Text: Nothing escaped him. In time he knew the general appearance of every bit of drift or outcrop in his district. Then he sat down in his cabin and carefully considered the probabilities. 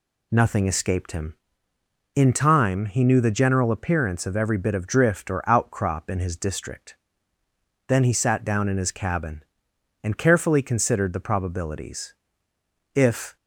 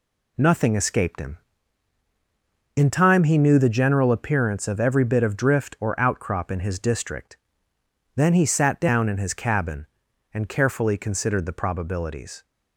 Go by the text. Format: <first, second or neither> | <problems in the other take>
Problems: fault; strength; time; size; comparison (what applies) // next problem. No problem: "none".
second | goes on to say "If"; slight; from 12.9 s on; 0.42 s long